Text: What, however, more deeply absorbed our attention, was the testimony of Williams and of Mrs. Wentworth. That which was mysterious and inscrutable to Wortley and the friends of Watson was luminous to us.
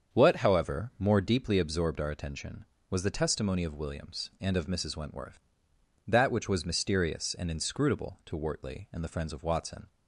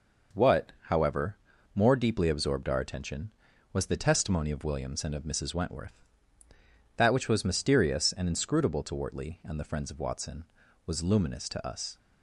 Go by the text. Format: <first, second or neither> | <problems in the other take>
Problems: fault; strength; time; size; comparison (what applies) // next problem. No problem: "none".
second | starts louder than the rest; strong; until 1.2 s; 7 dB // stops before "was luminous to us"; at 9.8 s